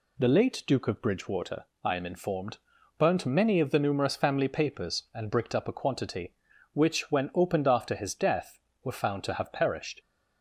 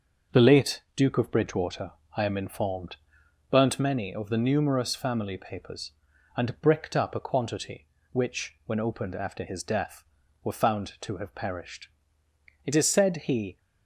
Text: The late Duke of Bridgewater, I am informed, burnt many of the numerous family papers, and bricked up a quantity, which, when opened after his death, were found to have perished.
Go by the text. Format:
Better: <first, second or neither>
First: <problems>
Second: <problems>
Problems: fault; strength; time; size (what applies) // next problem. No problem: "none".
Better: first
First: none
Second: starts louder than the rest; until 1.4 s; 6.5 dB // goes on to say "It is said he"; noticeable; from 12.6 s on; 0.94 s long